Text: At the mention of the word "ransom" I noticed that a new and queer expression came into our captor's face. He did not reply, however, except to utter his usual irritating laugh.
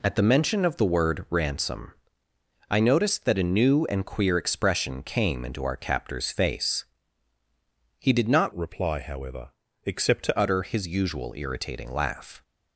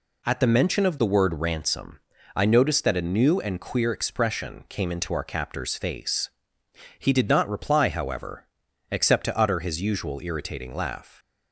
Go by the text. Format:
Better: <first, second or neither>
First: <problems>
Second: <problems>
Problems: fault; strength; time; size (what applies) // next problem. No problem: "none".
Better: second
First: pauses between "ransom" and "I"; noticeable; at 1.9 s; 0.78 s long // changes voice from "reply" to "to"; from 8.5 to 10.3 s; 1.8 s long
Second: pauses between "ransom" and "I"; slight; at 1.9 s; 0.34 s long